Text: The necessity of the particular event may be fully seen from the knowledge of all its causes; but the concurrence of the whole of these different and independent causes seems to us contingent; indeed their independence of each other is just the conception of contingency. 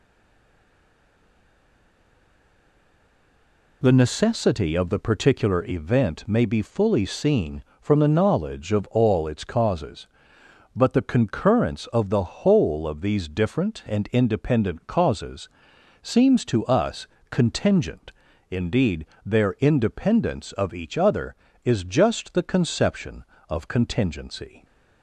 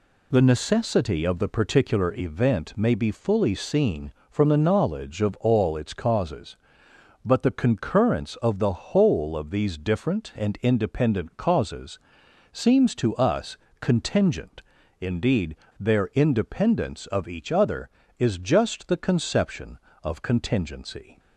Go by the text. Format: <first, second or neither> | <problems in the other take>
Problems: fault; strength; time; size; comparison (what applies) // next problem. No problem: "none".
second | stays silent before the first word; strong; until 3.8 s; 3.8 s long // pauses between "causes" and "seems"; noticeable; at 15.4 s; 0.54 s long; noticeable in the second // pauses between "us" and "contingent"; slight; at 17.0 s; 0.24 s long; slight in the second // pauses between "indeed" and "their"; slight; at 19.0 s; 0.22 s long; slight in the second